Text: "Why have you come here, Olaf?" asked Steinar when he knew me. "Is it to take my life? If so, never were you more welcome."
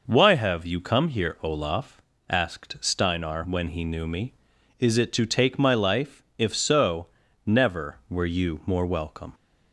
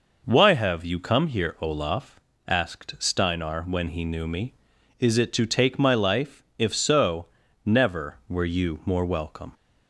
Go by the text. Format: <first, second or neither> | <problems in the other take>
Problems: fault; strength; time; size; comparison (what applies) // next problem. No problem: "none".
neither | none